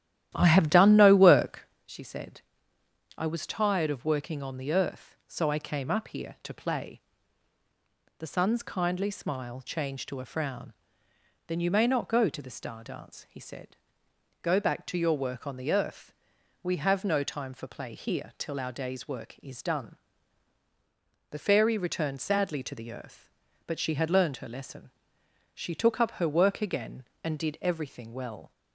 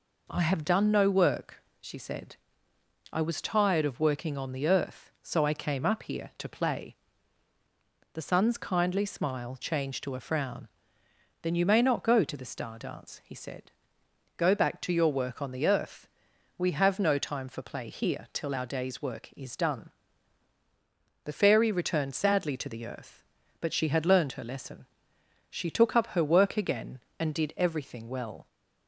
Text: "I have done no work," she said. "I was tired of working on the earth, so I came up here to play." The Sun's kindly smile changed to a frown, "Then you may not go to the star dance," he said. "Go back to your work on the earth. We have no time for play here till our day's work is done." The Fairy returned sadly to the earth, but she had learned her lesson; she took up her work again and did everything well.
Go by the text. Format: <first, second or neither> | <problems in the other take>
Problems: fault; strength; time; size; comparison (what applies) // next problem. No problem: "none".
second | starts louder than the rest; strong; until 1.7 s; 12.5 dB